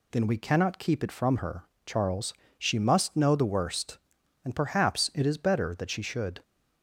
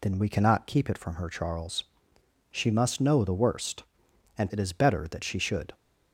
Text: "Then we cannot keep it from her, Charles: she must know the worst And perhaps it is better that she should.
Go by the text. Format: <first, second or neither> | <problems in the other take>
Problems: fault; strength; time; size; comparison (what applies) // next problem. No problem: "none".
first | skips "perhaps"; at 4.5 s